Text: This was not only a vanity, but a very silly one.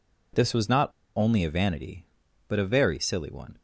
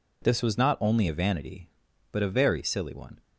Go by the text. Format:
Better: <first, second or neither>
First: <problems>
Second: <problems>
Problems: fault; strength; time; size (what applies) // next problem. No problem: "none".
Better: second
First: pauses between "not" and "only"; slight; at 0.8 s; 0.27 s long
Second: none